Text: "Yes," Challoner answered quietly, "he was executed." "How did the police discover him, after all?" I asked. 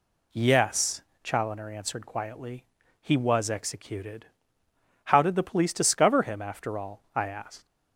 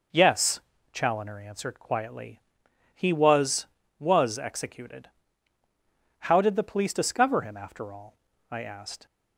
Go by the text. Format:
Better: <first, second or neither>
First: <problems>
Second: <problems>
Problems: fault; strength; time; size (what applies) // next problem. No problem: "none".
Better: first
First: none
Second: says "was" twice; at 3.9 s